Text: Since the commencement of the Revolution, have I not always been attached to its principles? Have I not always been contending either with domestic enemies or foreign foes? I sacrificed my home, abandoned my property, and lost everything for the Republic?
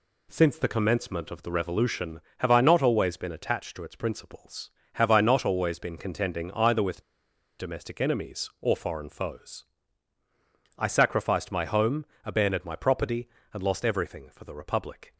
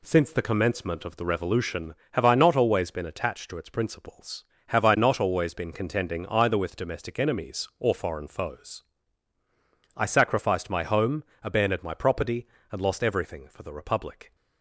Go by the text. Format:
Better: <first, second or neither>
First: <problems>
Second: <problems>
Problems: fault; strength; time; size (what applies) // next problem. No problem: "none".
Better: second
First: pauses between "with" and "domestic"; noticeable; at 7.0 s; 0.57 s long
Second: none